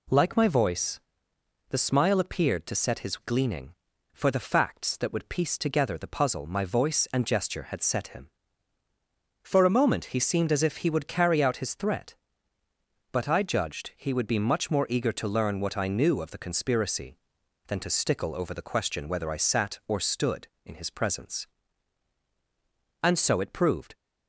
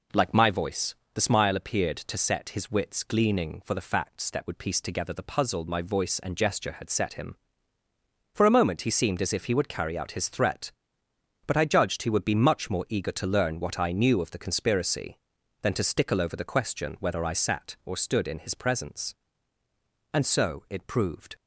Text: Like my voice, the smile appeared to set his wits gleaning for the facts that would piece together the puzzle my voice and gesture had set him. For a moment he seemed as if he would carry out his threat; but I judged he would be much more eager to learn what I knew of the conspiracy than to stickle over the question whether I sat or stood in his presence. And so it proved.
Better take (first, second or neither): second